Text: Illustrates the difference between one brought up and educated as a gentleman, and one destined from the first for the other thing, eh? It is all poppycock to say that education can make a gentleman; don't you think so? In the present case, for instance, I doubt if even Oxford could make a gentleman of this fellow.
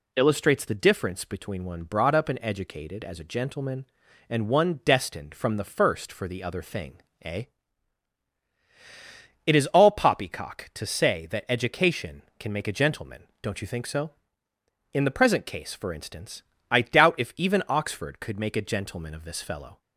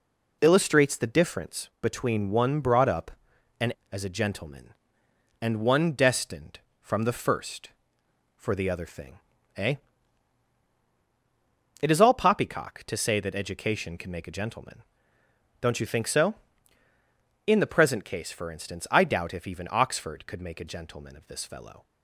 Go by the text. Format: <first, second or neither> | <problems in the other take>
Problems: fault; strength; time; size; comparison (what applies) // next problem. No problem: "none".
first | skips "educated"; at 3.8 s